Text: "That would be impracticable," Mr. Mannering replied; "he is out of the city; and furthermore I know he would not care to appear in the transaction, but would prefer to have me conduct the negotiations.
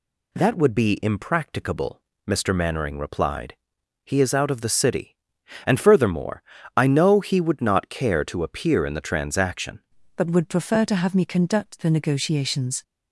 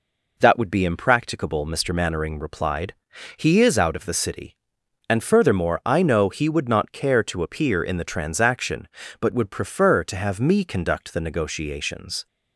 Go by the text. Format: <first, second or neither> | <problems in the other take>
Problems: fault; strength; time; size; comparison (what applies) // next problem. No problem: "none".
second | pauses between "furthermore" and "I"; slight; at 6.4 s; 0.32 s long // changes voice at "but"; from 10.1 s on; 2.7 s long